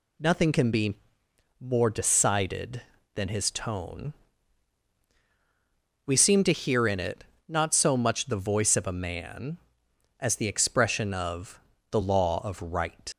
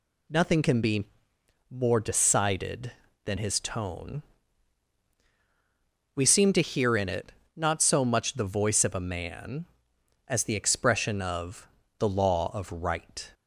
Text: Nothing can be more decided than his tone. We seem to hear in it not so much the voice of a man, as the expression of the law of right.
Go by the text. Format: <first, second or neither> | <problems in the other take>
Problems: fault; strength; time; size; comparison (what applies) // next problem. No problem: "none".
second | pauses between "be" and "more"; noticeable; at 0.9 s; 0.64 s long; noticeable in the second // pauses between "it" and "not"; slight; at 7.2 s; 0.24 s long; slight in the second // pauses between "of" and "the"; slight; at 11.5 s; 0.32 s long; slight in the second // leaves "right" unfinished; at 13.1 s; 110 ms